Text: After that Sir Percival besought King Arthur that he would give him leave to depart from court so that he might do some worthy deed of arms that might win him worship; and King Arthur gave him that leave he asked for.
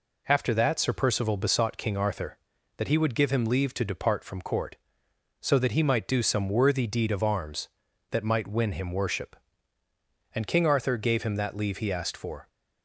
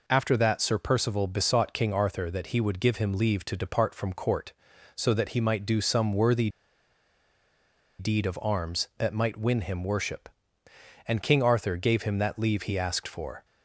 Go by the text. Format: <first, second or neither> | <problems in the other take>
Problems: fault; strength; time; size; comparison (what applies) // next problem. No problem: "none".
first | pauses between "worthy" and "deed"; strong; at 6.4 s; 1.5 s long